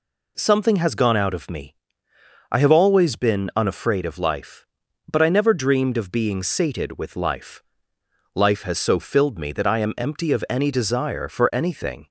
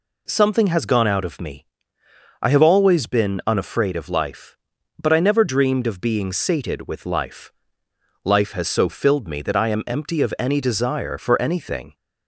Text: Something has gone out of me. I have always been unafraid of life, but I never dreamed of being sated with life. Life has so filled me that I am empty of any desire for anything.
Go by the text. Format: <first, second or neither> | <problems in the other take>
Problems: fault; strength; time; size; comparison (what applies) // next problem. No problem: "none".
neither | none